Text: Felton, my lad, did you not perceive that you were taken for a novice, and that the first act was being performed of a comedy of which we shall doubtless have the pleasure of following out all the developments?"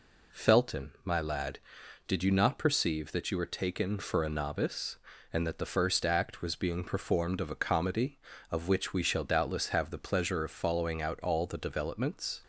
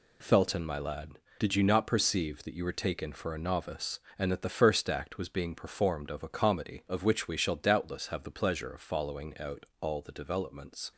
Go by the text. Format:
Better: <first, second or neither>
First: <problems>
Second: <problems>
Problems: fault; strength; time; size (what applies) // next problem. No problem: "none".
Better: neither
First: none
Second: none